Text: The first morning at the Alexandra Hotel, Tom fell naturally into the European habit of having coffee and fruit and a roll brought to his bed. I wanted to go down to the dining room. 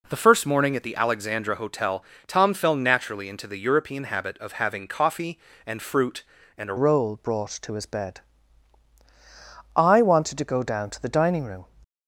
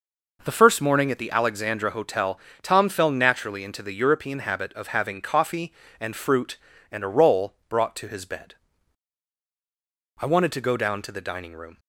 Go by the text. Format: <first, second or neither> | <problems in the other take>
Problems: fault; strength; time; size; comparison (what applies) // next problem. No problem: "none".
second | changes voice at "roll"; from 6.7 s on; 4.9 s long